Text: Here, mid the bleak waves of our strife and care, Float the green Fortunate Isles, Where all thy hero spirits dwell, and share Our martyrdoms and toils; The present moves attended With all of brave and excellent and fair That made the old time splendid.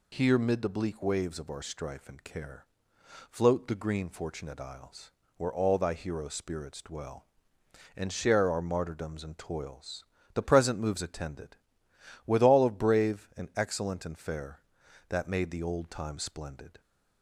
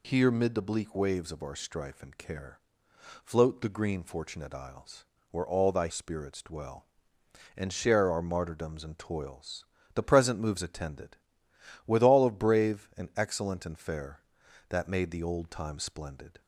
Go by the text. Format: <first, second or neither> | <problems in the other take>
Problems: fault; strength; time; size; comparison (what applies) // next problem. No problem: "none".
first | skips "hero"; at 5.8 s